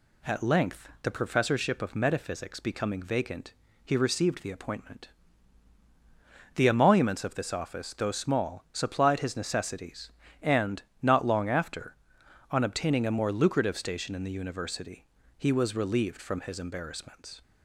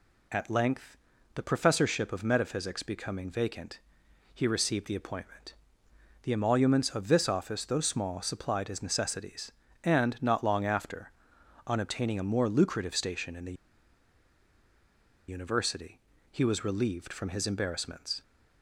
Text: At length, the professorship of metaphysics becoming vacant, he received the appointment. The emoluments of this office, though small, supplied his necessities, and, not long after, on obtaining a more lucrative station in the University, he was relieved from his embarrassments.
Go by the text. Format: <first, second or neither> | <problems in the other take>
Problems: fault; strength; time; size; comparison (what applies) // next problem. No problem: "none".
first | pauses between "the" and "University"; strong; at 13.5 s; 1.7 s long